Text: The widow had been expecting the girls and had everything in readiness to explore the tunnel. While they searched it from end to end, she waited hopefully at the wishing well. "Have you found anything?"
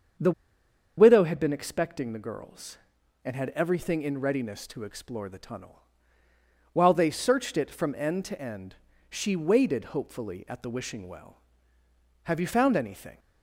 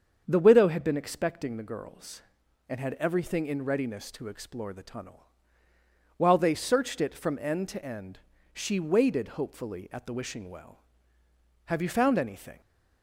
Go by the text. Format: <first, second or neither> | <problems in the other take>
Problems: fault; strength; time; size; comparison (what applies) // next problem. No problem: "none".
second | starts louder than the rest; strong; until 1.8 s; 7 dB; also in the second // pauses between "The" and "widow"; noticeable; at 0.3 s; 0.66 s long